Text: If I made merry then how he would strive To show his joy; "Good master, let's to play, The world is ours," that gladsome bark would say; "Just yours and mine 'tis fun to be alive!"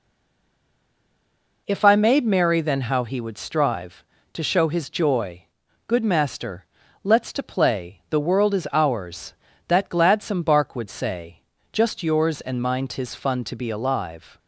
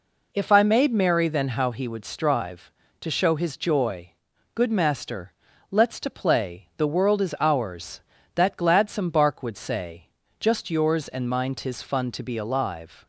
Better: second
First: stays silent before the first word; noticeable; until 1.6 s; 1.6 s long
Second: none

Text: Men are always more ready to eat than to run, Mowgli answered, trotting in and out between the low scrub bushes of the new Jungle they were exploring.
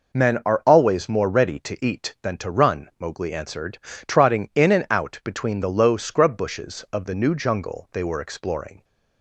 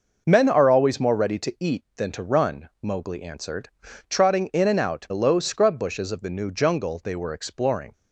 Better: first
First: none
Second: skips "between"; at 5.0 s

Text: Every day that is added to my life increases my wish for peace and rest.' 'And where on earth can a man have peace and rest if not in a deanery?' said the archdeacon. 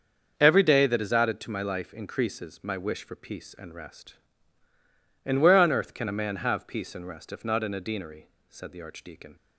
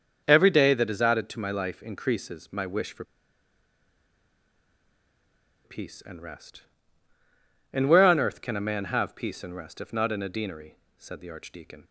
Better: first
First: starts louder than the rest; until 1.4 s; 6.5 dB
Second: starts louder than the rest; until 1.2 s; 6.5 dB // pauses between "for" and "peace"; strong; at 3.0 s; 2.6 s long

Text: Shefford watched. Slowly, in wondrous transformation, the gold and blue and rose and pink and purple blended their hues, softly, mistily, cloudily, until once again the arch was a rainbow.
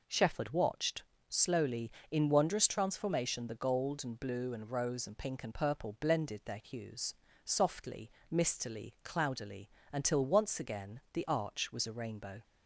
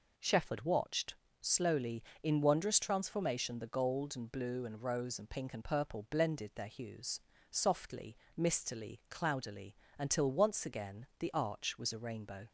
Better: neither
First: none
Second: none

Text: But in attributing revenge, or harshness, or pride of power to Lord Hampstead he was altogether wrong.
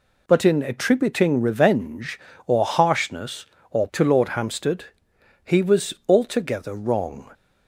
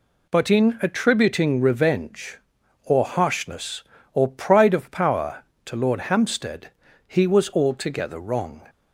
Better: second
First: skips "pride of power"; at 3.9 s // pauses between "Hampstead" and "he"; noticeable; at 4.8 s; 0.60 s long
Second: pauses between "Hampstead" and "he"; slight; at 6.6 s; 0.36 s long

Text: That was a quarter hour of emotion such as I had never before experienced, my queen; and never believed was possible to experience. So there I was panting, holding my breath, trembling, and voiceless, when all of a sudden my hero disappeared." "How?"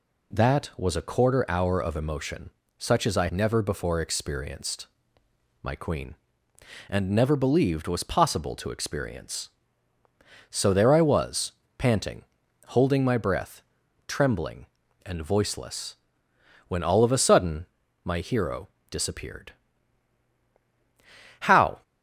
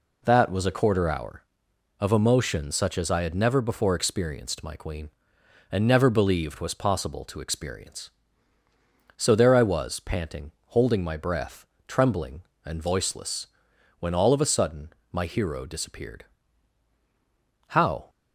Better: second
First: pauses between "emotion" and "such"; slight; at 2.4 s; 0.28 s long // skips "had"; at 3.2 s // pauses between "was" and "panting"; slight; at 11.5 s; 0.24 s long // pauses between "sudden" and "my"; at 17.6 s; 0.38 s long // pauses between "hero" and "disappeared"; slight; at 18.6 s; 0.22 s long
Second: pauses between "sudden" and "my"; slight; at 14.8 s; 0.22 s long

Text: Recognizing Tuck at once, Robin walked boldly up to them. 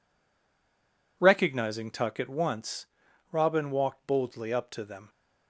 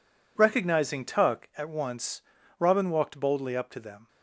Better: second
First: stays silent before the first word; noticeable; until 1.1 s; 1.1 s long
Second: none

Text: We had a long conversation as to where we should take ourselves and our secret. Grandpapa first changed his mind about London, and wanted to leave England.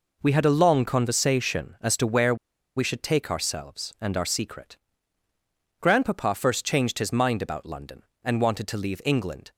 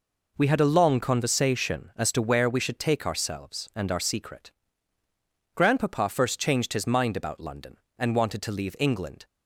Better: second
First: pauses between "where" and "we"; at 2.3 s; 0.41 s long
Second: none

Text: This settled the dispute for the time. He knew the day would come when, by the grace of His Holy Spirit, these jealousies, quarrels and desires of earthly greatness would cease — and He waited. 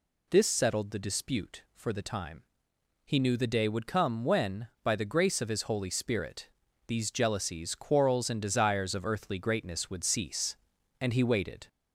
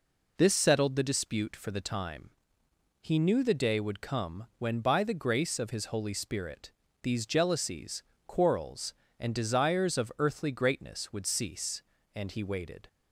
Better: second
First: gets louder; slight; throughout; 2.5 dB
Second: none

